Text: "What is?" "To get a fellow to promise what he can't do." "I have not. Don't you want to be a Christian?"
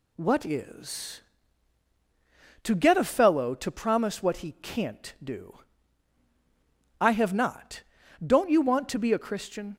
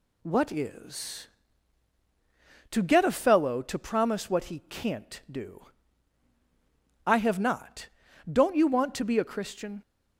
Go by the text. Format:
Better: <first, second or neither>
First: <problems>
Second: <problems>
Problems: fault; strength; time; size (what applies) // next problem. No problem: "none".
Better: neither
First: none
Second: none